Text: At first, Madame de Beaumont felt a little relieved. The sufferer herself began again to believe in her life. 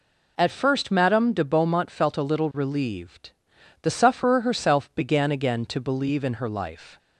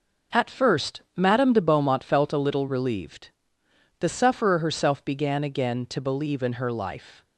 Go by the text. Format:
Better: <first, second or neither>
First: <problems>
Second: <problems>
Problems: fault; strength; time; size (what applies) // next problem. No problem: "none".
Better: neither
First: none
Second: none